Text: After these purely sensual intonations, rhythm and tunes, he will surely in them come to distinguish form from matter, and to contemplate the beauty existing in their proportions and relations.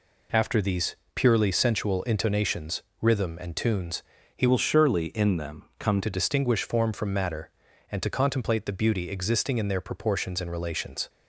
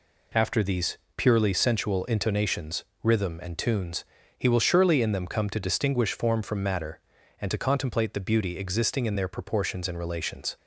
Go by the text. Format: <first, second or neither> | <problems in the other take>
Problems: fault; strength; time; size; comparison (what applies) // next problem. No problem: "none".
second | pauses between "these" and "purely"; slight; at 0.9 s; 0.20 s long; slight in the second // changes voice from "will" to "come"; from 4.4 to 5.9 s; 1.5 s long